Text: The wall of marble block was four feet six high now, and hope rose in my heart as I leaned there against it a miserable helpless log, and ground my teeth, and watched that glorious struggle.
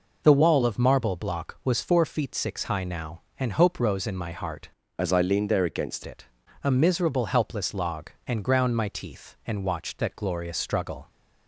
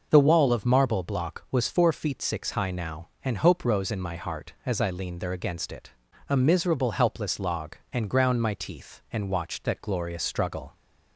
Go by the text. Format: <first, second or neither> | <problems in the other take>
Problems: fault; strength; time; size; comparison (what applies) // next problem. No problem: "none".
second | changes voice from "as" to "against"; from 4.9 to 6.0 s; 1.1 s long // pauses between "it" and "a"; slight; at 6.2 s; 0.36 s long; slight in the second